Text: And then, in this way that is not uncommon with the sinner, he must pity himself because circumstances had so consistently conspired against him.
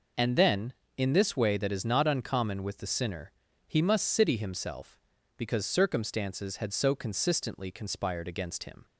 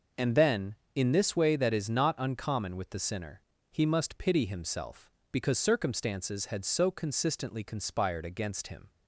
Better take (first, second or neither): second